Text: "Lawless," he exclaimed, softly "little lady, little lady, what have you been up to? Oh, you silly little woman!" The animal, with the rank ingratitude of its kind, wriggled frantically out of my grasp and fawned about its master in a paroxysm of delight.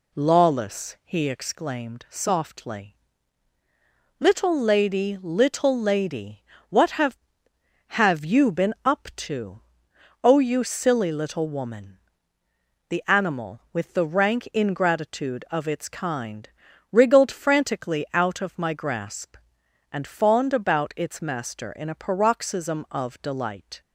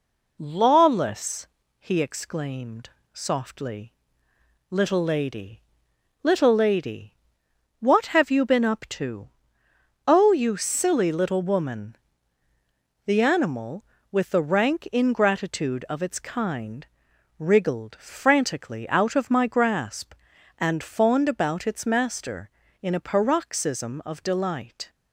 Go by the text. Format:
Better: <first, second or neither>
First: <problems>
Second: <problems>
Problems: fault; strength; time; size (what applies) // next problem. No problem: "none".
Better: second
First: pauses between "softly" and "little"; at 2.9 s; 1.2 s long // says "have" twice; at 7.9 s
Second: pauses between "softly" and "little"; noticeable; at 3.9 s; 0.78 s long